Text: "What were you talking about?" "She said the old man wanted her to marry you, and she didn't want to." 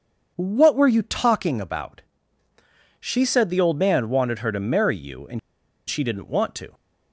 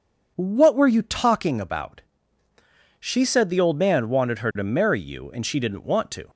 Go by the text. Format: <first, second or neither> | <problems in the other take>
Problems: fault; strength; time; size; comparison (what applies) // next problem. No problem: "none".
second | pauses between "and" and "she"; noticeable; at 5.3 s; 0.50 s long